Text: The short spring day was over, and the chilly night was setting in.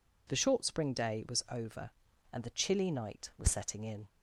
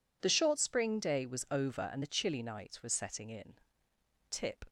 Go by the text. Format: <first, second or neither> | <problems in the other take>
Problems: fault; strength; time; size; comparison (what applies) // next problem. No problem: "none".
first | goes on to say "Tip"; slight; from 4.2 s on; 0.36 s long